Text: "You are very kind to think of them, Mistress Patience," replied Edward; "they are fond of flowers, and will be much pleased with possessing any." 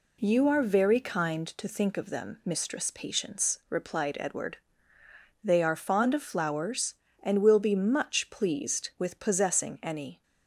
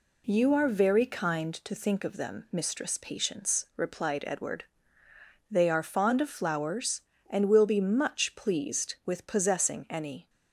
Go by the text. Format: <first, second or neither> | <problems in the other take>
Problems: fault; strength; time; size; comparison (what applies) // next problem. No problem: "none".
neither | none